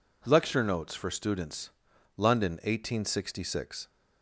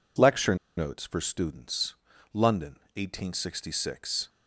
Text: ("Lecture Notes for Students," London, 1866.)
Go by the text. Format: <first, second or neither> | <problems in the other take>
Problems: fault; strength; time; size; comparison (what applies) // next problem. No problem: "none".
first | pauses between "Lecture" and "Notes"; slight; at 0.5 s; 0.22 s long